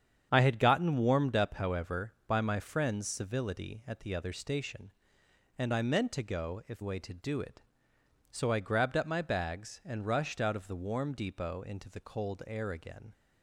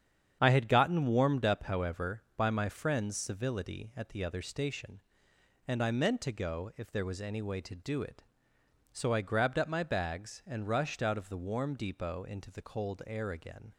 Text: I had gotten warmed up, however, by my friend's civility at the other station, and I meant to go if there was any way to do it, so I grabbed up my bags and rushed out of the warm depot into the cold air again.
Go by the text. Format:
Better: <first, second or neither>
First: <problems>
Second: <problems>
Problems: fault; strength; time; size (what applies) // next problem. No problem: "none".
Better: second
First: starts louder than the rest; strong; until 1.3 s; 8.5 dB // skips "there was any"; at 6.8 s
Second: starts louder than the rest; strong; until 1.4 s; 8 dB